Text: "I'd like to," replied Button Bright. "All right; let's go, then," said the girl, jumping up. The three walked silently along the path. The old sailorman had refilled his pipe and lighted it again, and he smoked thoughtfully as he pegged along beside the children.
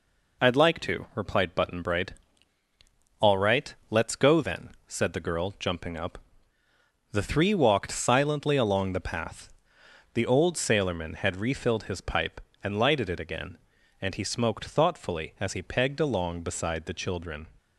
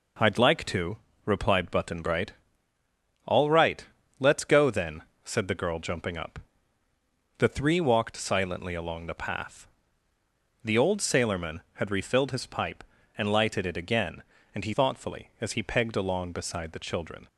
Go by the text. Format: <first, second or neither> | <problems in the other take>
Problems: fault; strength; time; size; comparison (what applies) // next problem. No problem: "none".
first | skips "smoked"; at 14.7 s